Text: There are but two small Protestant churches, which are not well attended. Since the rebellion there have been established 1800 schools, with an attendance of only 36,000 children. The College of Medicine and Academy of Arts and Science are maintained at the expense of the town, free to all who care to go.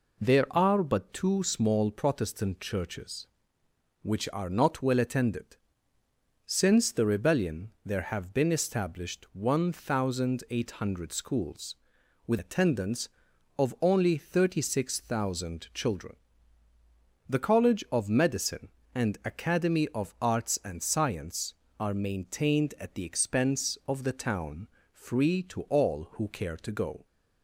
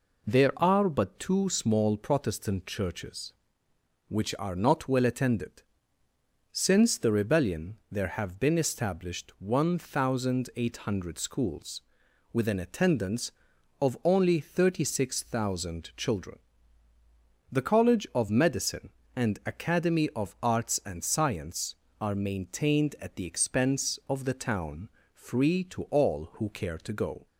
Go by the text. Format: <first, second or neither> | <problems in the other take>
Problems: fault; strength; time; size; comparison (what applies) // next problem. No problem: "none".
second | pauses between "rebellion" and "there"; slight; at 7.6 s; 0.16 s long; slight in the second // skips "an"; at 12.3 s